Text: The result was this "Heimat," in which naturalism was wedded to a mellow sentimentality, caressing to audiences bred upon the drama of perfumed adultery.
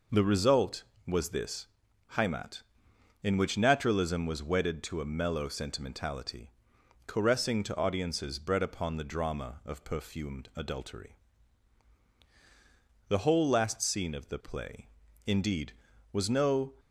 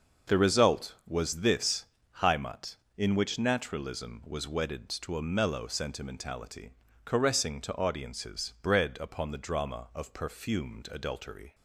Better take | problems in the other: second | pauses between "this" and "Heimat"; noticeable; at 1.6 s; 0.48 s long; slight in the second // goes on to say "The whole last scene of the play indeed was no"; strong; from 13.0 s on; 3.6 s long

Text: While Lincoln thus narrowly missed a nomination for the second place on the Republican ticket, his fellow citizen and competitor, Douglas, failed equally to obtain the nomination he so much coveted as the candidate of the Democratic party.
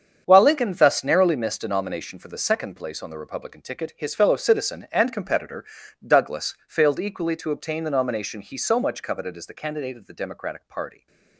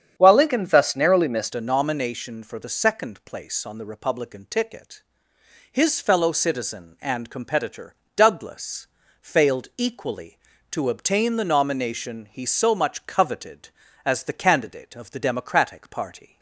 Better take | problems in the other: first | starts louder than the rest; strong; until 1.1 s; 8 dB; strong in the first // changes voice at "a"; from 1.5 s on; 14.8 s long

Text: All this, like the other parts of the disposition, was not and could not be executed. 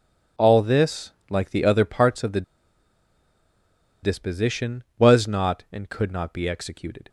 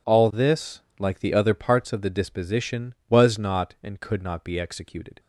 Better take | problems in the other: second | pauses between "the" and "disposition"; strong; at 2.4 s; 1.6 s long

